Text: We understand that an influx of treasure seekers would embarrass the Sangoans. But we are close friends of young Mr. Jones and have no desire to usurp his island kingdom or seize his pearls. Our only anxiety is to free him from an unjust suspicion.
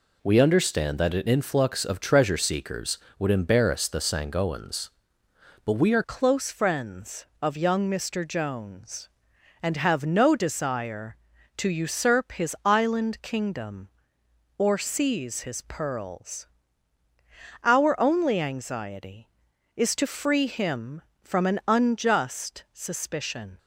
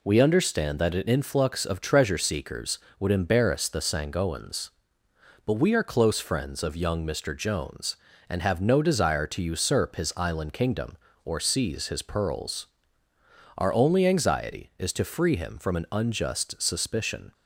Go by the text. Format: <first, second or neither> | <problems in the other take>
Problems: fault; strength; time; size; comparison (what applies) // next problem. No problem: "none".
second | changes voice at "close"; from 6.0 s on; 17.5 s long